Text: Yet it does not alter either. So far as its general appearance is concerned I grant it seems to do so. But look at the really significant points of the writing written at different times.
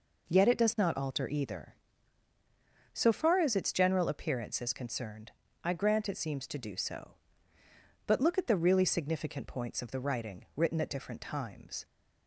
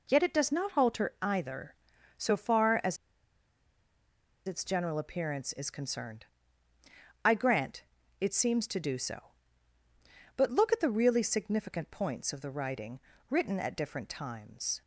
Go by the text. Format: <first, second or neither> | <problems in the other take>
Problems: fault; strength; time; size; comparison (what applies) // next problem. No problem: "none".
first | pauses between "as" and "its"; strong; at 2.9 s; 1.5 s long // pauses between "concerned" and "I"; at 6.2 s; 1.0 s long; slight in the first // pauses between "grant" and "it"; at 7.8 s; 0.38 s long // pauses between "writing" and "written"; slight; at 12.9 s; 0.30 s long